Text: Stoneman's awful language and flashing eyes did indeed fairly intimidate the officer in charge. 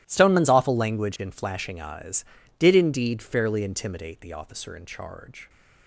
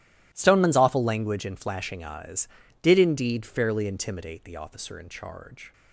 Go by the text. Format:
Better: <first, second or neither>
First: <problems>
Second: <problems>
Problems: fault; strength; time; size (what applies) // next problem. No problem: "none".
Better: neither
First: starts louder than the rest; strong; until 1.0 s; 15 dB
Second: starts louder than the rest; strong; until 1.3 s; 15.5 dB